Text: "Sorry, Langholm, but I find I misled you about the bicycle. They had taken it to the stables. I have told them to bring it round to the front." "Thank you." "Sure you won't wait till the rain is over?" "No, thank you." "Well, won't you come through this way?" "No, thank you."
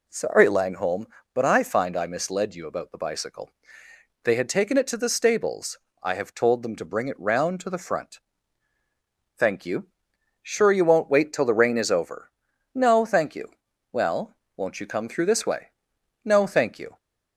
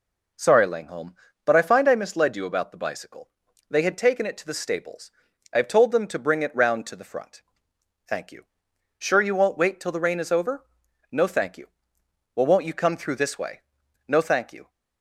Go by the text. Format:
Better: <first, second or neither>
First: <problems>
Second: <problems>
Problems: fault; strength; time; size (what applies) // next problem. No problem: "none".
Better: neither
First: none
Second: none